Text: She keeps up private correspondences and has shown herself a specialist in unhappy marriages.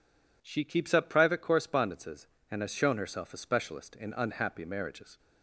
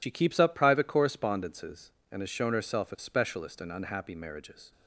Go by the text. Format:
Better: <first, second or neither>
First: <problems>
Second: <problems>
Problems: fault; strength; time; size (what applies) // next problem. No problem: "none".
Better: first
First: none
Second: loses the start of "She"; at 0.0 s; 70 ms